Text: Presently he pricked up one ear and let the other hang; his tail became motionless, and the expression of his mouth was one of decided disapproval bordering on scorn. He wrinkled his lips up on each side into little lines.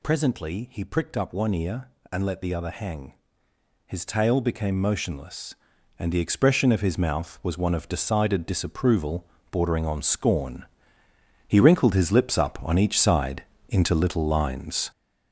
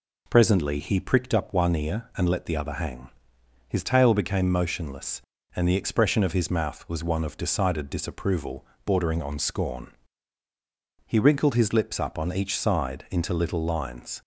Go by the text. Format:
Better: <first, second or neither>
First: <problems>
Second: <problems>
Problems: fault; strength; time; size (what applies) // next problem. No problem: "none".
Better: second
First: gets louder; throughout; 7 dB // pauses between "disapproval" and "bordering"; slight; at 9.2 s; 0.28 s long // pauses between "side" and "into"; slight; at 13.4 s; 0.26 s long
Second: pauses between "disapproval" and "bordering"; slight; at 8.6 s; 0.20 s long